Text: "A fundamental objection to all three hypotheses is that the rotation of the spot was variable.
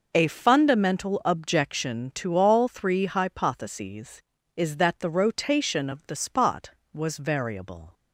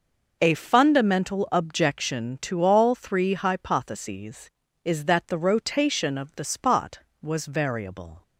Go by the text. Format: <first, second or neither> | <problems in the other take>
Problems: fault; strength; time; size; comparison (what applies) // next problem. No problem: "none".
neither | none